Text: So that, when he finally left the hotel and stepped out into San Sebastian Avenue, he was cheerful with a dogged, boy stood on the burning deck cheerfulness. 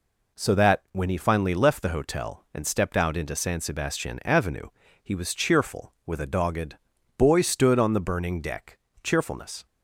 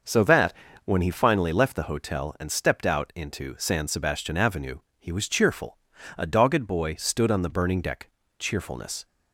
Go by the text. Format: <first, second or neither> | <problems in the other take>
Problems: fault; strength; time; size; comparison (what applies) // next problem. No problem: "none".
first | starts louder than the rest; noticeable; until 1.3 s; 6 dB // skips "with"; at 5.9 s // pauses between "deck" and "cheerfulness"; slight; at 8.0 s; 0.28 s long; slight in the first